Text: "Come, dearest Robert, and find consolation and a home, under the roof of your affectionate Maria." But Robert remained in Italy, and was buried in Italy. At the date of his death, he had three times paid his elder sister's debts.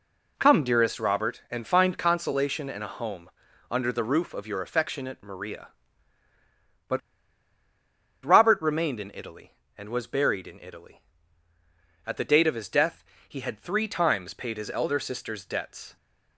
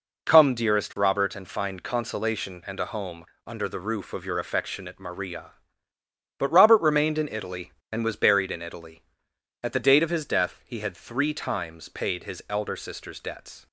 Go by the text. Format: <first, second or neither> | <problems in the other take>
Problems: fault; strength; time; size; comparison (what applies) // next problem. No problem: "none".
second | pauses between "But" and "Robert"; at 7.0 s; 1.2 s long